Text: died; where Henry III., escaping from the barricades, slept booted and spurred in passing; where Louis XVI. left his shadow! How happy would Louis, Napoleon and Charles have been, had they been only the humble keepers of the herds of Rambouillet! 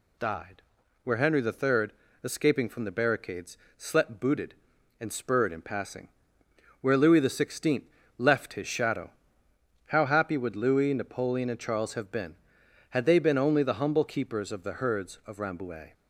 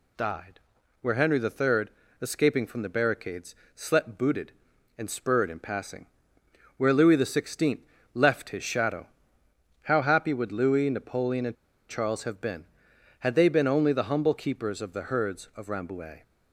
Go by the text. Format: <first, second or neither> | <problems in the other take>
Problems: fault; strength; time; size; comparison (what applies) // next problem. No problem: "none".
first | pauses between "and" and "Charles"; slight; at 11.5 s; 0.33 s long